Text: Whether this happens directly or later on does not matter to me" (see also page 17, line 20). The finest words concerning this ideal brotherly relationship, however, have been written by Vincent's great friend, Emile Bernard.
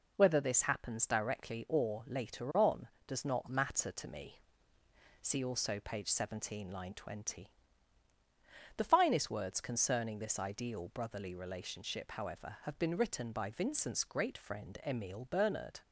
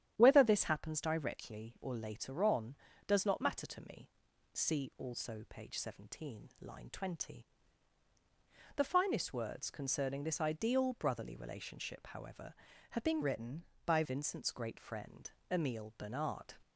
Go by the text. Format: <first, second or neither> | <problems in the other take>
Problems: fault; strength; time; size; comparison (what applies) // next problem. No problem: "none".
first | starts louder than the rest; strong; until 1.1 s; 10 dB // changes voice from "written" to "by"; from 13.2 to 14.0 s; 0.8 s long